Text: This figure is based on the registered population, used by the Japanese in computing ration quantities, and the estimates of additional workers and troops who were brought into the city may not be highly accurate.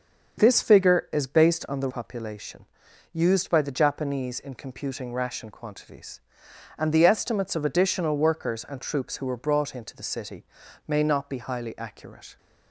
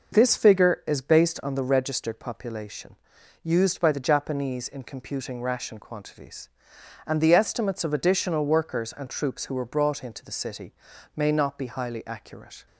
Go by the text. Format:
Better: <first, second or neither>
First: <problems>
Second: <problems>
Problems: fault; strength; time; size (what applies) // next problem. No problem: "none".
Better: second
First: starts louder than the rest; until 1.4 s; 6.5 dB // skips "registered"; at 1.8 s // pauses between "city" and "may"; at 10.4 s; 0.42 s long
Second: pauses between "city" and "may"; at 10.7 s; 0.42 s long